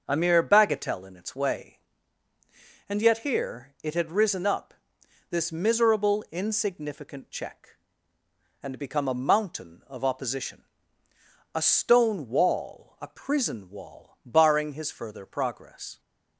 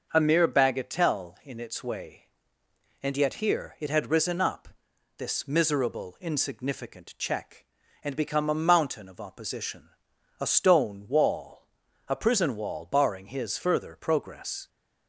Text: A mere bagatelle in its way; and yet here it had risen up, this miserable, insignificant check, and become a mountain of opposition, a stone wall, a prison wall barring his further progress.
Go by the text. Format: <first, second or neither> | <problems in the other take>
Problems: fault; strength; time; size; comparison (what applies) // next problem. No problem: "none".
neither | starts louder than the rest; the same in both